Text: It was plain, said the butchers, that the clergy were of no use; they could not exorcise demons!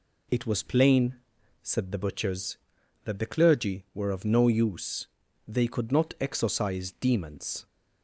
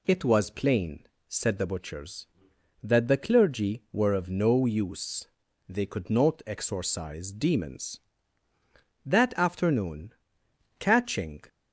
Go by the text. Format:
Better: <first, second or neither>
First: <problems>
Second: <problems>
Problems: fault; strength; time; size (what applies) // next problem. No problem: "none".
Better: first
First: none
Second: goes on to say "That afternoon catching"; strong; from 9.0 s on; 2.3 s long